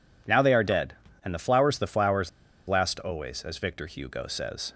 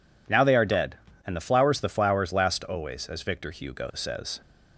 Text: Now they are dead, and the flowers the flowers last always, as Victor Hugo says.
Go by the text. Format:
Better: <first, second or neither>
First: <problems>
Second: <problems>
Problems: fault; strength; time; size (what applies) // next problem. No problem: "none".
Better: second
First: pauses between "flowers" and "last"; at 2.2 s; 0.37 s long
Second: none